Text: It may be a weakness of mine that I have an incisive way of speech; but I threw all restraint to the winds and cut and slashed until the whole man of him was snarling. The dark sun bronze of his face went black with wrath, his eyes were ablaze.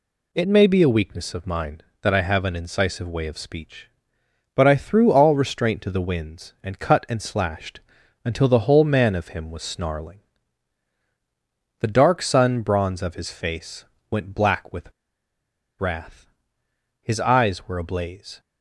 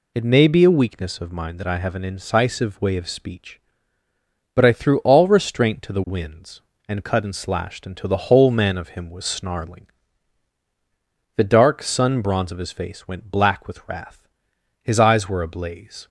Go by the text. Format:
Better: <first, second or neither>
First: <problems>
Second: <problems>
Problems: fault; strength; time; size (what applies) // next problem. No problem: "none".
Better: second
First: pauses between "slashed" and "until"; at 7.8 s; 0.42 s long // pauses between "face" and "went"; slight; at 13.8 s; 0.26 s long // pauses between "with" and "wrath"; noticeable; at 14.9 s; 0.87 s long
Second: none